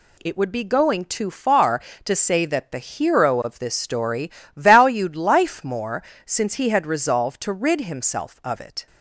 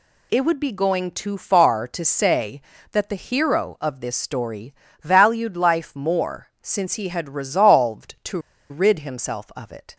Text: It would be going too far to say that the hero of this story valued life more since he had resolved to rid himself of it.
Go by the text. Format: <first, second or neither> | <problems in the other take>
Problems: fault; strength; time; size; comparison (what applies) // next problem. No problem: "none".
first | pauses between "story" and "valued"; slight; at 4.7 s; 0.30 s long; slight in the first // pauses between "more" and "since"; slight; at 6.4 s; 0.16 s long; slight in the first // pauses between "to" and "rid"; slight; at 8.3 s; 0.31 s long